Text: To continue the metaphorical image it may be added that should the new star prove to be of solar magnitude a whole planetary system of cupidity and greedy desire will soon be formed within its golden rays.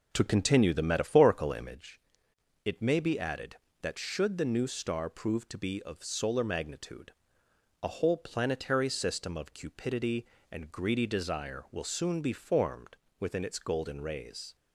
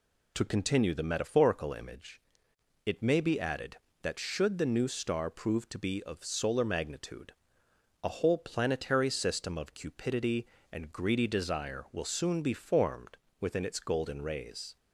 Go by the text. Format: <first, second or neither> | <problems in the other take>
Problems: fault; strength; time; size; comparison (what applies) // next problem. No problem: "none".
second | starts louder than the rest; noticeable; until 1.9 s; 4 dB // pauses between "image" and "it"; noticeable; at 2.0 s; 0.64 s long; noticeable in the second // pauses between "magnitude" and "a"; noticeable; at 7.1 s; 0.68 s long; noticeable in the second // pauses between "formed" and "within"; slight; at 12.9 s; 0.22 s long; slight in the second